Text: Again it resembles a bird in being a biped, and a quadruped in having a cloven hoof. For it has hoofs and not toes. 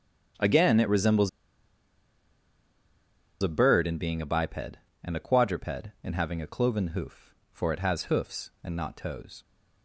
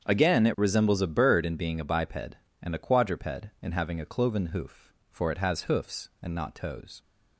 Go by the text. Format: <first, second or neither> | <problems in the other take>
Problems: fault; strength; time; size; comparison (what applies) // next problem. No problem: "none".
second | starts louder than the rest; strong; until 3.5 s; 7.5 dB; strong in the second // pauses between "resembles" and "a"; strong; at 1.2 s; 2.1 s long